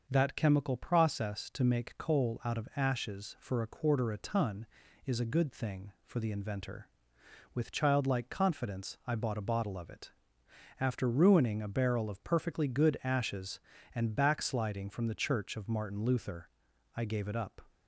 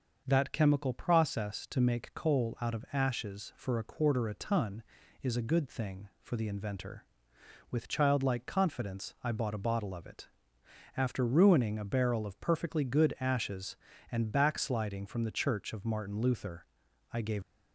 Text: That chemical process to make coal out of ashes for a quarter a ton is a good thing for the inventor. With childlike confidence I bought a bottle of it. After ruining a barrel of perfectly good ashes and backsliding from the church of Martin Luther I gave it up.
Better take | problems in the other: first | starts louder than the rest; noticeable; until 1.2 s; 6 dB; also in the first // pauses between "Luther" and "I"; noticeable; at 16.6 s; 0.46 s long; noticeable in the first // stops before "it up"; at 17.4 s

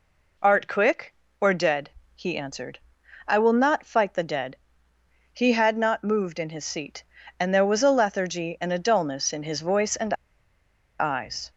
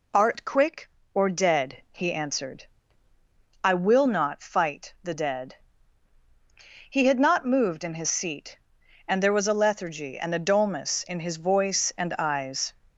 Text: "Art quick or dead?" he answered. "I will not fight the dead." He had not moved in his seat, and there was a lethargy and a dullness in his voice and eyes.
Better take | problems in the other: second | pauses between "and" and "eyes"; noticeable; at 10.1 s; 0.86 s long

